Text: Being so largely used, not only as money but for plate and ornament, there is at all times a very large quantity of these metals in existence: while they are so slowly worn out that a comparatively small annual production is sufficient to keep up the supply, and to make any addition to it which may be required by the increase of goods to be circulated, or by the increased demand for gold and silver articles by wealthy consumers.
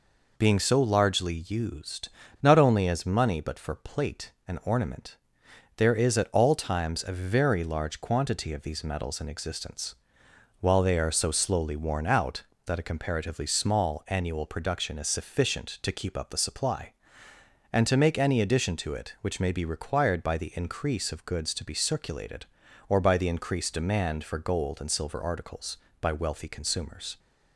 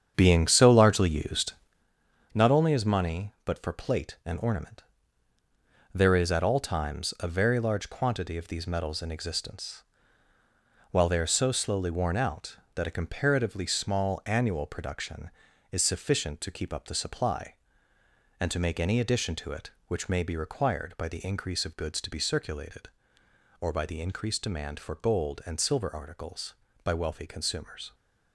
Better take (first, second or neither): first